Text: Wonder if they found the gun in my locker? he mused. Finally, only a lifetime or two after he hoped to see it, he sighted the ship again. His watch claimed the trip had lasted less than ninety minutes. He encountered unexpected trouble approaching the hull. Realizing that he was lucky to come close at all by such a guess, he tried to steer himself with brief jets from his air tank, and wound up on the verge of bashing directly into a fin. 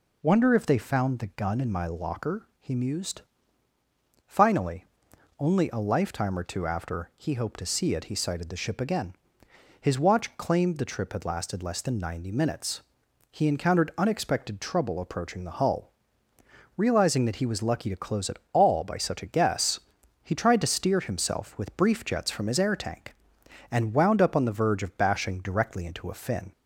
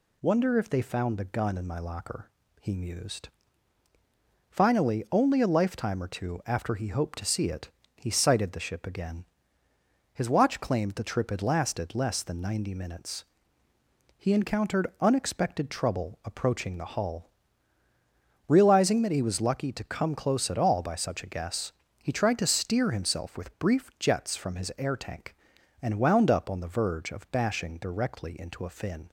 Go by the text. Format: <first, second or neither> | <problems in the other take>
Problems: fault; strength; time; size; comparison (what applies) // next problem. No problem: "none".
second | skips "come"; at 17.9 s